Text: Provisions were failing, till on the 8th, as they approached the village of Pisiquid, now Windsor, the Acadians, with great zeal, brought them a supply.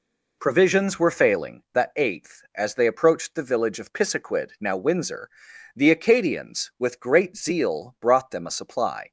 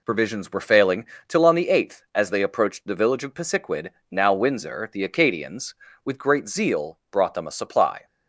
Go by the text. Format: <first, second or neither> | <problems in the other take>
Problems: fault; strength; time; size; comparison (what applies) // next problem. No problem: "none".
second | skips "till on"; at 1.6 s